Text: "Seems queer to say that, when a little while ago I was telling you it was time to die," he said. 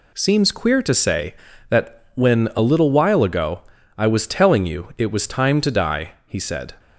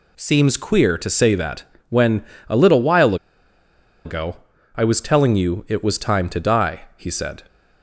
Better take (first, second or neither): first